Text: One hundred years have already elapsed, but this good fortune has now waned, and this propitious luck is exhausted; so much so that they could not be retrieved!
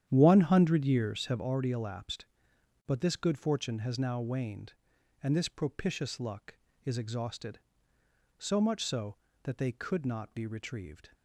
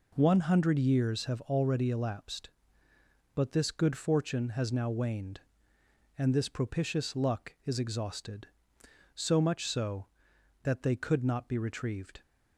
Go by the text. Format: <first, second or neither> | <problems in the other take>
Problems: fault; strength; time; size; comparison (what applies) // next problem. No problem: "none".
second | starts louder than the rest; strong; until 1.4 s; 10 dB